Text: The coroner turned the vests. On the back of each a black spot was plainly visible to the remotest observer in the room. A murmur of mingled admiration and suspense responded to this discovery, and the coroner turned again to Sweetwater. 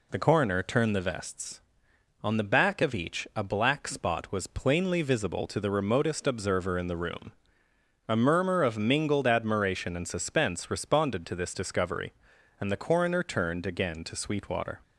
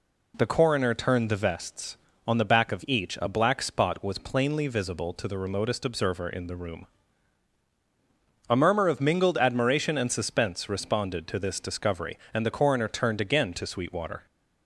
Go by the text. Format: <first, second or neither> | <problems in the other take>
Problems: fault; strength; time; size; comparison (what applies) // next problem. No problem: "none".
neither | none